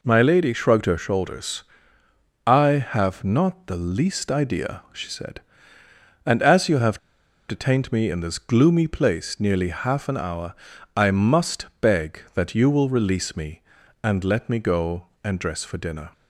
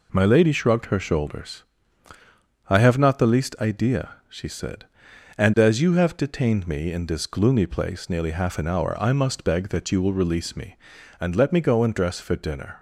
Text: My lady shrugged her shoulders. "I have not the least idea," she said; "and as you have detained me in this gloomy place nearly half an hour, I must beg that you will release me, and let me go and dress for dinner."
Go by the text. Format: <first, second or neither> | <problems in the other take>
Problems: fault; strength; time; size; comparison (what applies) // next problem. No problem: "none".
second | pauses between "have" and "detained"; noticeable; at 6.9 s; 0.49 s long // pauses between "must" and "beg"; slight; at 11.6 s; 0.16 s long